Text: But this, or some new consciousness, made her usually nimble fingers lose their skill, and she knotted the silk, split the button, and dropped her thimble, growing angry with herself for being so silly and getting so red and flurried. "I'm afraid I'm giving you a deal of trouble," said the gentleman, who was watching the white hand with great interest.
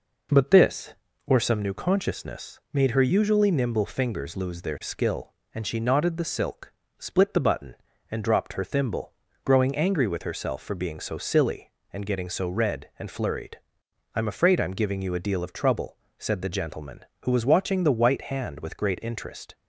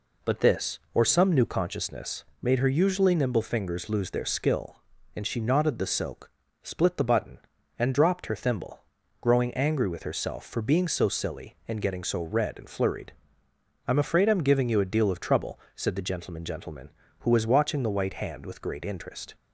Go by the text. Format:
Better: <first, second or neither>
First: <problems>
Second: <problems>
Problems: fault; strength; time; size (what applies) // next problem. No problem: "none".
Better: first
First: none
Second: says "gentleman" twice; at 16.4 s